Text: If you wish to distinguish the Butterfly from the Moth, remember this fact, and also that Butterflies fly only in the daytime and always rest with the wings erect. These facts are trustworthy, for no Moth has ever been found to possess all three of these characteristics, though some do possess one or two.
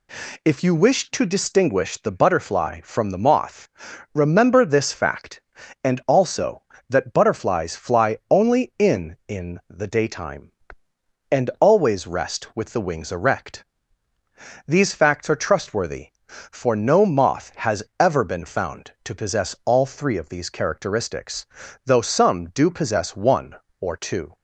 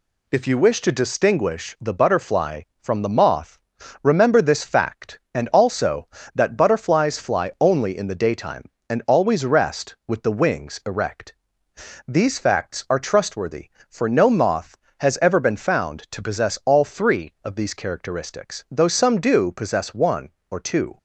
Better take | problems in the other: second | says "in" twice; at 9.2 s // pauses between "has" and "ever"; slight; at 17.8 s; 0.16 s long

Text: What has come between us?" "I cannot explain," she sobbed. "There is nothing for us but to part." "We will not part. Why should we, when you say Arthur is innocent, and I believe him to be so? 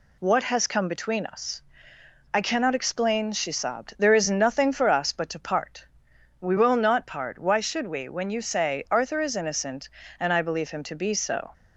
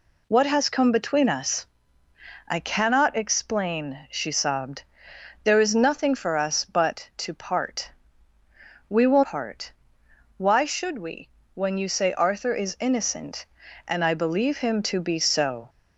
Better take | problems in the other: first | skips "not"; at 9.2 s

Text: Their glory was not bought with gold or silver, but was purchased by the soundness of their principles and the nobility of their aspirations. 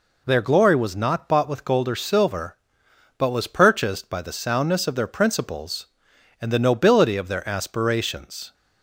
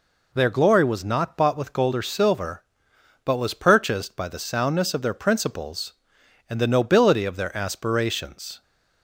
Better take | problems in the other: neither | none

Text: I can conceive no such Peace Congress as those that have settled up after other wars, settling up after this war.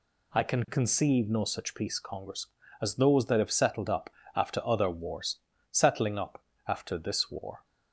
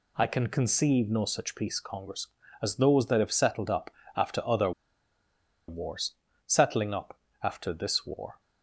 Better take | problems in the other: first | pauses between "up" and "after"; slight; at 3.9 s; 0.24 s long; slight in the first // pauses between "other" and "wars"; noticeable; at 4.7 s; 0.97 s long // pauses between "up" and "after"; slight; at 7.1 s; 0.24 s long; slight in the first

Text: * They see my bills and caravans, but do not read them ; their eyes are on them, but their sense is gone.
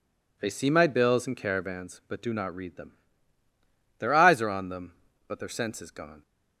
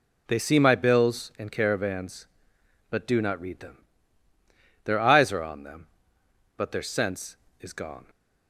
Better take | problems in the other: neither | none

